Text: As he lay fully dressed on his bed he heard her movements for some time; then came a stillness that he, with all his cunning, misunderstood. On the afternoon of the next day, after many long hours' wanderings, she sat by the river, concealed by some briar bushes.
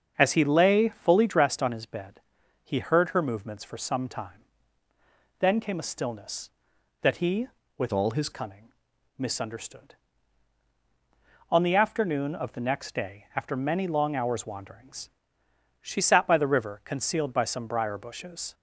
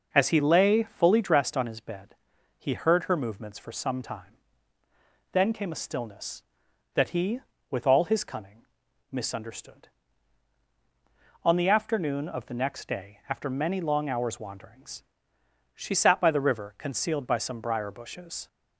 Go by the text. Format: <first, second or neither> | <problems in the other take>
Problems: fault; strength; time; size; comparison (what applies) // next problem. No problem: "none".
second | starts louder than the rest; until 1.1 s; 6.5 dB // pauses between "bed" and "he"; at 2.2 s; 0.42 s long; also in the second // changes voice from "all" to "his"; from 7.9 to 8.2 s; 0.3 s long